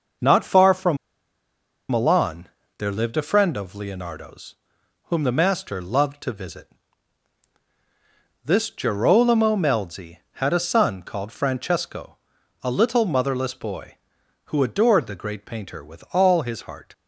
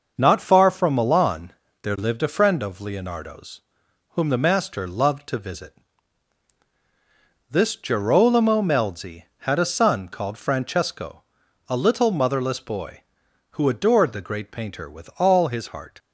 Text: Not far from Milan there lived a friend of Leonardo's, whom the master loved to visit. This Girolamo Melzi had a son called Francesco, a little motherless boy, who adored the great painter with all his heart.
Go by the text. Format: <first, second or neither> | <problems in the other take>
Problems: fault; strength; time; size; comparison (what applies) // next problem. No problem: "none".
second | pauses between "from" and "Milan"; noticeable; at 0.9 s; 0.92 s long // pauses between "Milan" and "there"; slight; at 2.4 s; 0.30 s long; slight in the second